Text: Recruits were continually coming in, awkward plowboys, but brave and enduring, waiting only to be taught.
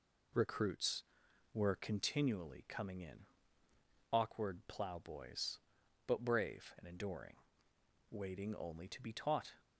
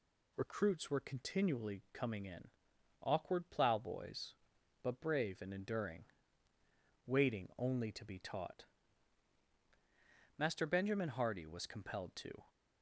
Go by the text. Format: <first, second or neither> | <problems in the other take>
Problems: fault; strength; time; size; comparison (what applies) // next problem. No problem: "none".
first | goes on to say "Master Benjamin Hardy was compelled to"; strong; from 10.3 s on; 2.0 s long